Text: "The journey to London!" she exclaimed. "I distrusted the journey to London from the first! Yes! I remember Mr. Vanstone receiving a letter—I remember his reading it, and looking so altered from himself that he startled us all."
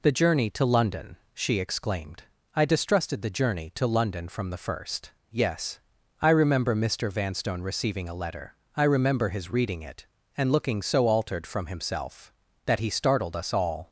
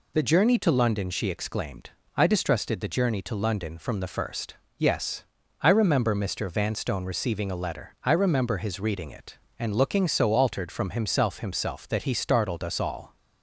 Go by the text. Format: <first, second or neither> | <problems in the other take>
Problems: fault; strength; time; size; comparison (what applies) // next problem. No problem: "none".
first | says "himself" twice; at 11.4 s